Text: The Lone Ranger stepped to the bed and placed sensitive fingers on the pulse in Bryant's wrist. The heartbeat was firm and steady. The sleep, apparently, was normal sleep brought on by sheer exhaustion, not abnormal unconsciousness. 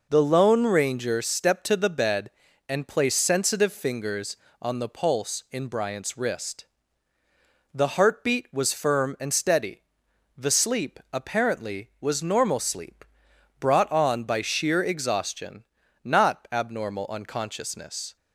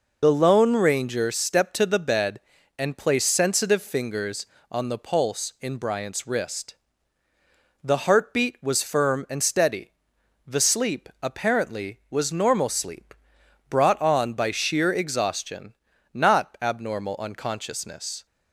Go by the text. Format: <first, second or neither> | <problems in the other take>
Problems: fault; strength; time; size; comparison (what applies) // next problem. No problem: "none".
first | loses the start of "The"; at 0.2 s; 35 ms // pauses between "sleep" and "brought"; noticeable; at 13.1 s; 0.54 s long; noticeable in the first